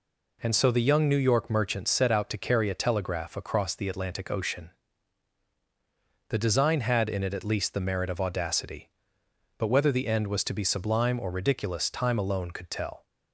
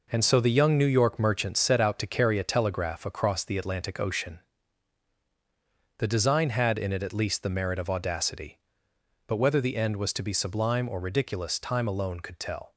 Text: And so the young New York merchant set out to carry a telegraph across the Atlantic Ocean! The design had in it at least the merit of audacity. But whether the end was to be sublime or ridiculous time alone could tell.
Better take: first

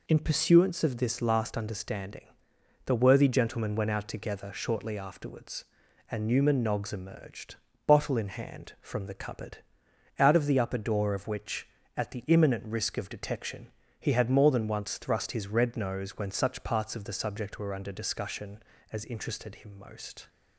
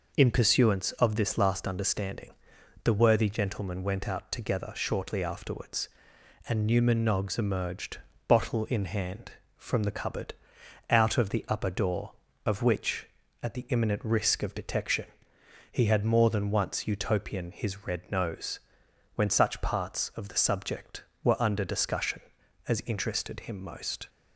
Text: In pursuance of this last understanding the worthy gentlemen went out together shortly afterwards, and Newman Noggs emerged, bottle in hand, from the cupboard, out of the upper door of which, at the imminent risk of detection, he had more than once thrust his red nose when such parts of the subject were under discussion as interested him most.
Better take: first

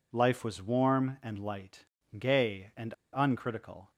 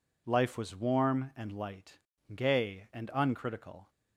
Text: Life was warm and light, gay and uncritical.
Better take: second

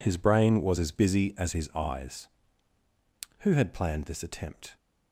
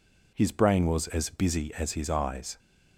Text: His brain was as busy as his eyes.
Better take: second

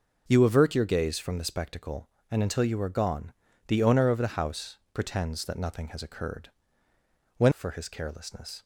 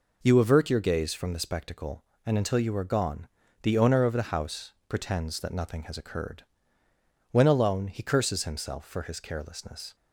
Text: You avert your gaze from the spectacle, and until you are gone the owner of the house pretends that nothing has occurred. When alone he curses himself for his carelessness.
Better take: second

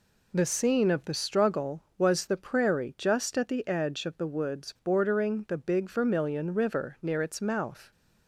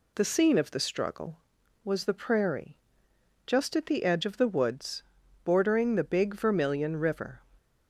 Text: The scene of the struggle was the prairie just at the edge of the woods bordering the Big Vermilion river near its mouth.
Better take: first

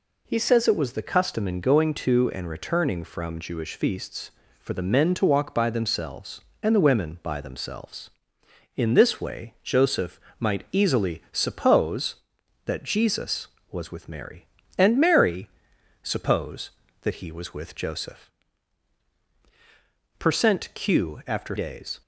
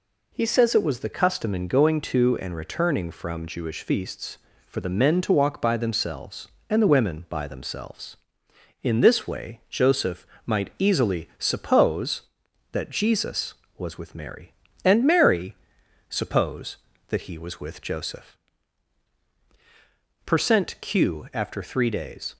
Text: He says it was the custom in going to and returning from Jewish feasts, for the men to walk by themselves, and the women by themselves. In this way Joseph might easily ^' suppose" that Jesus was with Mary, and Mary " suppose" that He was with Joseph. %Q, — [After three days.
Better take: second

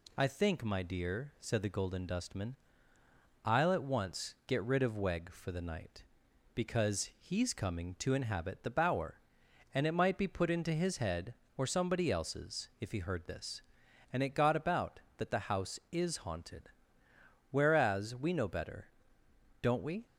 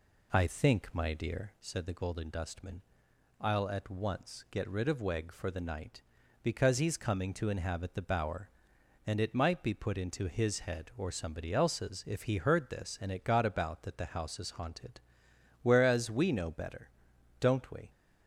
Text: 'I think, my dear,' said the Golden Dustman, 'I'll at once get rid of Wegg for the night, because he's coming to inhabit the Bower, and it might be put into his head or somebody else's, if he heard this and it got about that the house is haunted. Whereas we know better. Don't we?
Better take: first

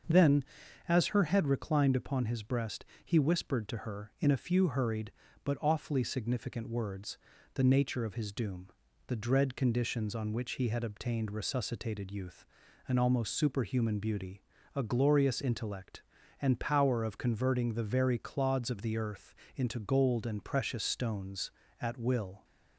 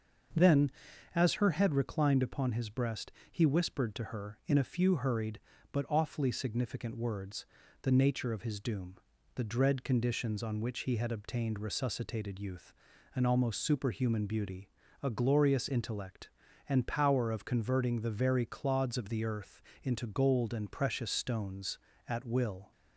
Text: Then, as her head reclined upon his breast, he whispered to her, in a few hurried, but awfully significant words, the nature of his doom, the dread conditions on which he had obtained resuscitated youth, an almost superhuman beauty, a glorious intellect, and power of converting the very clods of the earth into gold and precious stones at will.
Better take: neither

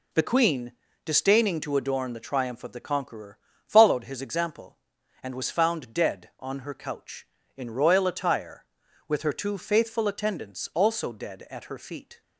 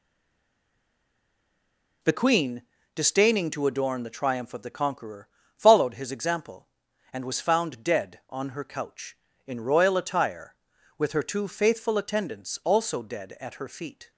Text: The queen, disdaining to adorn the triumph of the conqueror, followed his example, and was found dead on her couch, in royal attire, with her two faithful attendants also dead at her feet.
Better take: first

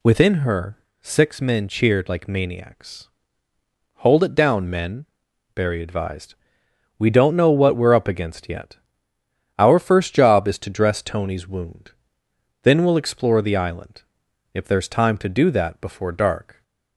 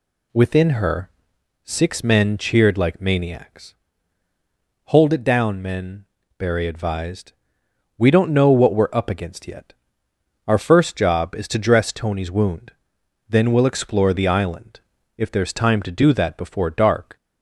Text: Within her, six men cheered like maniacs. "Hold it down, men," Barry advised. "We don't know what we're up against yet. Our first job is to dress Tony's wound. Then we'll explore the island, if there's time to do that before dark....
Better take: neither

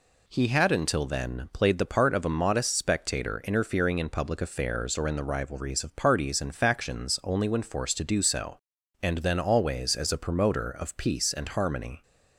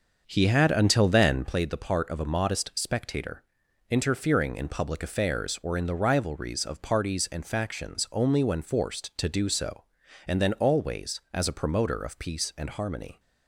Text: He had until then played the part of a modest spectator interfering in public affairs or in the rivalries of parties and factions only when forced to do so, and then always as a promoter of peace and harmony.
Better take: first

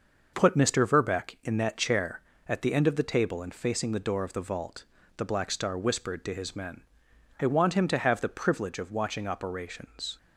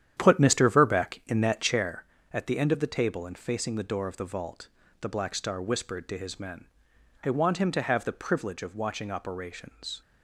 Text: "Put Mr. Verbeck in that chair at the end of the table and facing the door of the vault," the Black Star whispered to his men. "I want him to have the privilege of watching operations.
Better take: first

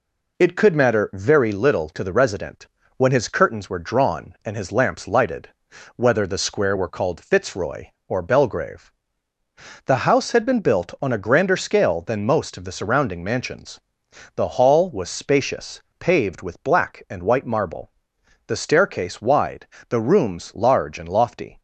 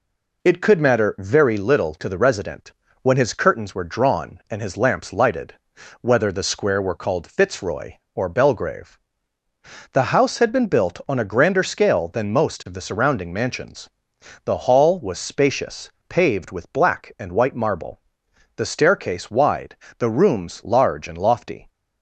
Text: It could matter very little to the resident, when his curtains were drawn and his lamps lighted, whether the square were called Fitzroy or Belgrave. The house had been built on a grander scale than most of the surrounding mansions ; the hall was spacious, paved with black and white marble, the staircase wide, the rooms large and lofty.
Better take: neither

